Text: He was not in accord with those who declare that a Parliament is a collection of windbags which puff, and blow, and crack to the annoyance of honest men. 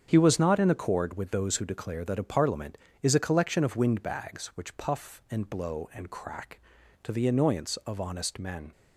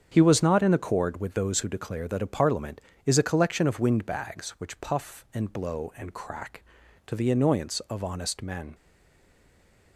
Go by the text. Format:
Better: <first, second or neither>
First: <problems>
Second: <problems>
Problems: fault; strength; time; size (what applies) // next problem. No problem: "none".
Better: first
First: starts louder than the rest; strong; until 1.1 s; 7.5 dB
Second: starts louder than the rest; strong; until 1.1 s; 7.5 dB // stays silent after the last word; noticeable; from 8.7 s on; 1.2 s long